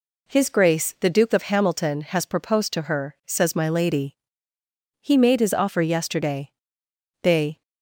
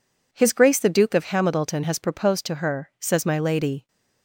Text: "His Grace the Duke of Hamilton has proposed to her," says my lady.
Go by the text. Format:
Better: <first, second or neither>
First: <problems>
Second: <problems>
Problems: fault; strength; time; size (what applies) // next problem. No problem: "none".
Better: second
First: goes on to say "He made his offer yesterday They"; strong; from 4.9 s on; 2.6 s long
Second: none